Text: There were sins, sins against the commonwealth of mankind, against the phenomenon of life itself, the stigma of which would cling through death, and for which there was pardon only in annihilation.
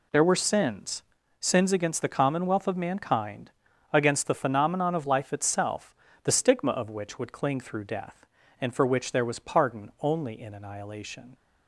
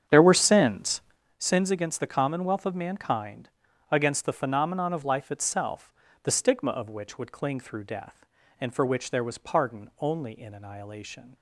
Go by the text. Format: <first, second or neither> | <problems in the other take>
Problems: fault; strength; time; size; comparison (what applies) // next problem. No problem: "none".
first | starts louder than the rest; strong; until 1.4 s; 8.5 dB